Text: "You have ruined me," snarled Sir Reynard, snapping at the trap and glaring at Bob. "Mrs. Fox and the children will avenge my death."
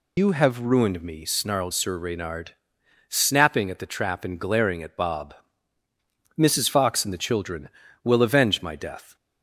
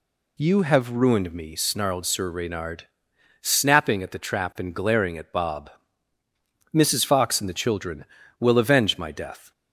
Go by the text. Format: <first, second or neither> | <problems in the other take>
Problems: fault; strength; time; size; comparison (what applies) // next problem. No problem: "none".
second | loses the start of "You"; at 0.1 s; 90 ms